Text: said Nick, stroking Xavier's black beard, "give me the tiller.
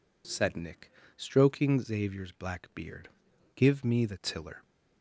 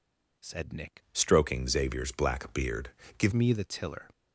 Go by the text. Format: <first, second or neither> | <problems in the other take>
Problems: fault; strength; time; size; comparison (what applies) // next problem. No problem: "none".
first | changes voice from "stroking" to "give"; from 1.1 to 3.3 s; 2.2 s long